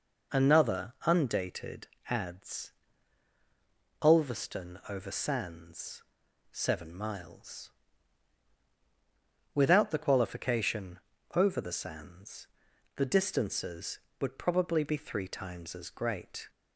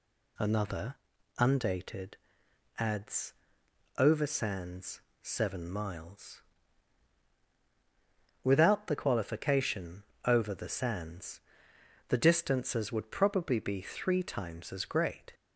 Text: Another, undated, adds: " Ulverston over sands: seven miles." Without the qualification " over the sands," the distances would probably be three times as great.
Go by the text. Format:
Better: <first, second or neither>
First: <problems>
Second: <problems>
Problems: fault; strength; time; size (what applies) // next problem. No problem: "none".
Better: first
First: none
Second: skips "Ulverston"; at 3.9 s